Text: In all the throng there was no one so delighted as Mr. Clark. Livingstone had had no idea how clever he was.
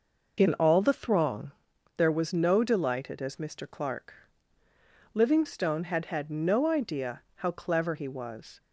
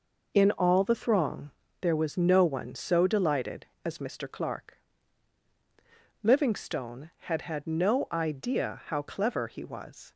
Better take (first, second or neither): second